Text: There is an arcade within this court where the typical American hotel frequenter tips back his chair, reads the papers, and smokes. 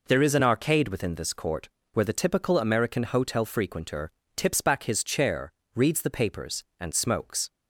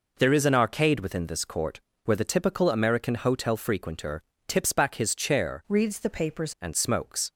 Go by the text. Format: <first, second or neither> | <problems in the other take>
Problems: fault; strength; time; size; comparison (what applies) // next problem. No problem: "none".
first | pauses between "court" and "where"; slight; at 1.8 s; 0.24 s long; slight in the first // pauses between "frequenter" and "tips"; slight; at 4.2 s; 0.26 s long; slight in the first // changes voice from "reads" to "papers"; from 5.6 to 6.5 s; 0.9 s long